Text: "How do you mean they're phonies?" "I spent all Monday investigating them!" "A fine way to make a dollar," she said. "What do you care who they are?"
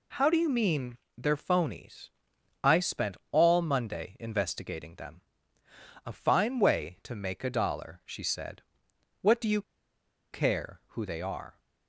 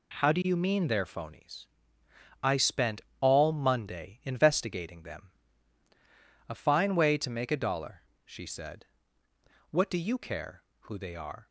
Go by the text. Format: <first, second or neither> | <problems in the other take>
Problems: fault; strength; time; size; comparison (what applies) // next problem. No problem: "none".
second | pauses between "mean" and "they're"; slight; at 0.9 s; 0.20 s long // pauses between "spent" and "all"; slight; at 3.1 s; 0.16 s long; slight in the second // pauses between "you" and "care"; noticeable; at 9.6 s; 0.70 s long